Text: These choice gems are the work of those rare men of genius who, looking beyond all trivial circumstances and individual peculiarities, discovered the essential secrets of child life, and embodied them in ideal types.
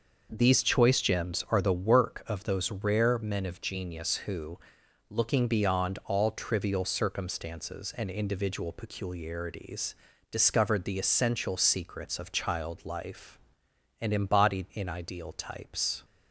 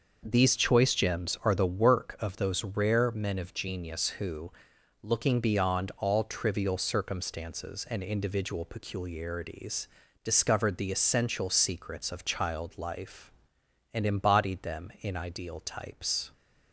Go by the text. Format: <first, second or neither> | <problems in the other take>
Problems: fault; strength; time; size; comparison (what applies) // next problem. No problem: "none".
second | starts louder than the rest; noticeable; until 1.3 s; 6 dB; noticeable in the second // skips "them"; at 14.7 s